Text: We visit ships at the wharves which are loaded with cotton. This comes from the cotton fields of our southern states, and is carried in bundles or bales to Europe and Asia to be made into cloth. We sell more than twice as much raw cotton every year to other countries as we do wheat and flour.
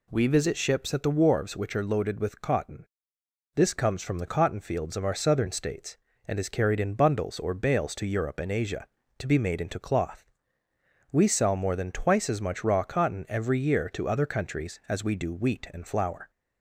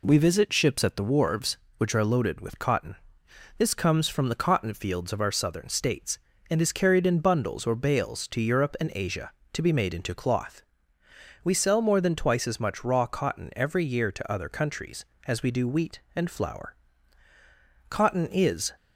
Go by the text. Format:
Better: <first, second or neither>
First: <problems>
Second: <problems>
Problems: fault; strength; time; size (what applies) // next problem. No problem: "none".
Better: first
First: none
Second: goes on to say "Cotton is"; noticeable; from 17.8 s on; 0.86 s long